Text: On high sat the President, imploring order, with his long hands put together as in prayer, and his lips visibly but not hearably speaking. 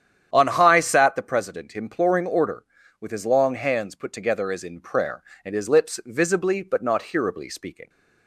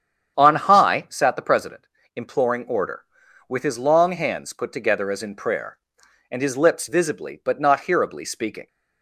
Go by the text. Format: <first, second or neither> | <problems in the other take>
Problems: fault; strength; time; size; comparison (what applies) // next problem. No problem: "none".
neither | starts louder than the rest; strong; the same in both